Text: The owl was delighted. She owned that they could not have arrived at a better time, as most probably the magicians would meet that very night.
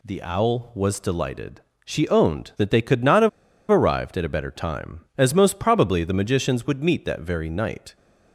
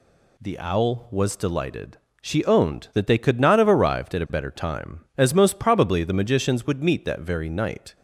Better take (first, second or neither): second